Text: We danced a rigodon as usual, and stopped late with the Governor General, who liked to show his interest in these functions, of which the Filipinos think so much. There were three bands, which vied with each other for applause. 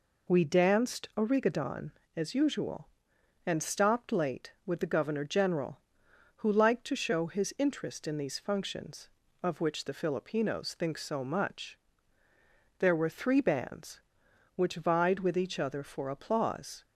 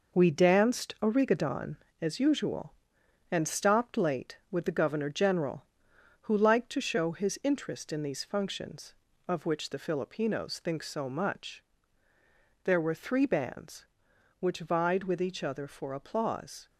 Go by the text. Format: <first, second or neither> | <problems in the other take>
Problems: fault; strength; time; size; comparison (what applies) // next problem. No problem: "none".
first | gets quieter; throughout; 7 dB